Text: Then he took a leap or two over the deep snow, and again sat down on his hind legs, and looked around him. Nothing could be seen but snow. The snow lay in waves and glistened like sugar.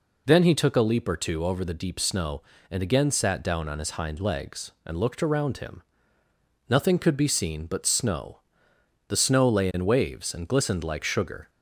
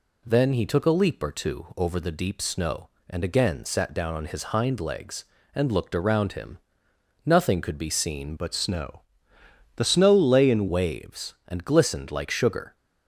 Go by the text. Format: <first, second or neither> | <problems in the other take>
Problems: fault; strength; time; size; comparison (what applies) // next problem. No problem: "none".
first | changes voice from "but" to "in"; from 8.3 to 10.6 s; 2.3 s long